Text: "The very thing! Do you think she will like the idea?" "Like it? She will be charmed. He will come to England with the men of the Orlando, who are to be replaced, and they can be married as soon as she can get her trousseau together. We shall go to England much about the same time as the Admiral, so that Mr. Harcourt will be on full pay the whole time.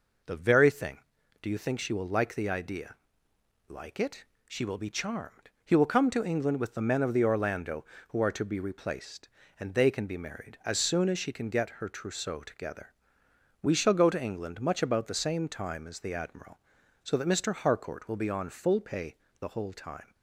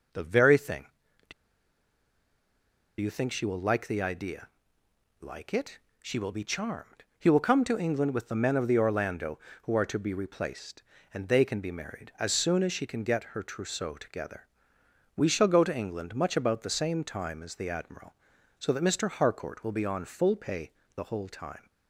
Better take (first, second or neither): first